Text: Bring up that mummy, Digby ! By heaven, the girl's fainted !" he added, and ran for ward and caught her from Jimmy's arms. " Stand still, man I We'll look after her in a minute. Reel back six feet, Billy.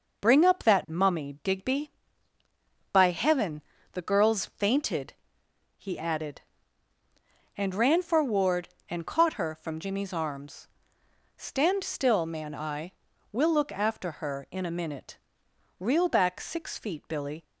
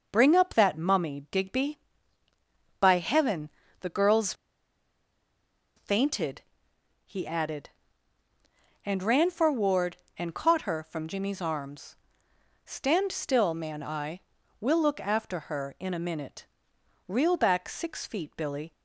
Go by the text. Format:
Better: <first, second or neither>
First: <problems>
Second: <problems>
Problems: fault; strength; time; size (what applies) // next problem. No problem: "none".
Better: first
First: starts louder than the rest; until 1.2 s; 6.5 dB // pauses between "I" and "We'll"; at 12.9 s; 0.40 s long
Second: starts louder than the rest; until 1.1 s; 6 dB // pauses between "girl's" and "fainted"; strong; at 4.3 s; 1.4 s long // pauses between "I" and "We'll"; at 14.1 s; 0.40 s long